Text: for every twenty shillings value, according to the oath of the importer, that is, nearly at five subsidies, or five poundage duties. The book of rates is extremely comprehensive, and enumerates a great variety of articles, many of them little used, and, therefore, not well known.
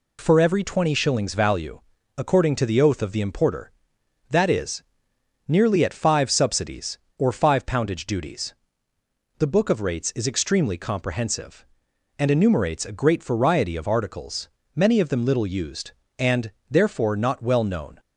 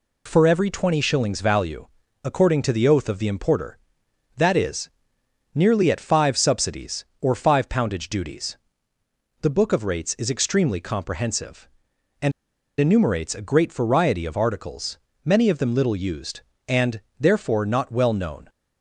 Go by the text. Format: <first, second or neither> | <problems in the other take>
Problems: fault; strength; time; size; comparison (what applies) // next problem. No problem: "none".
first | pauses between "and" and "enumerates"; noticeable; at 12.3 s; 0.49 s long